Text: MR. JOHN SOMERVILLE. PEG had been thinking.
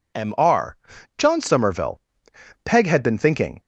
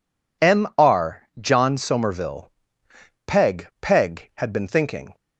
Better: first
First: none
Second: says "PEG" twice; at 3.8 s

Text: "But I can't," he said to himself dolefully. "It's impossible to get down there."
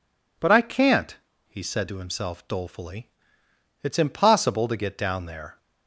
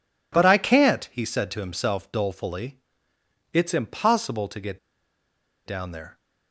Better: first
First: none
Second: pauses between "get" and "down"; noticeable; at 4.7 s; 0.86 s long

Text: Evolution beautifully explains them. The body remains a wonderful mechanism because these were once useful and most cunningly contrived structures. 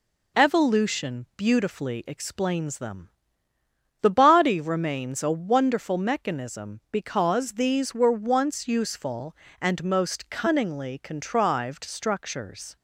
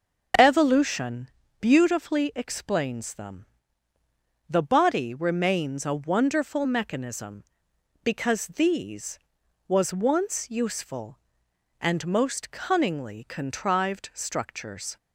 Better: first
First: none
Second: starts louder than the rest; until 1.7 s; 6.5 dB // pauses between "Evolution" and "beautifully"; slight; at 1.2 s; 0.32 s long // says "was" for "were"; at 9.6 s

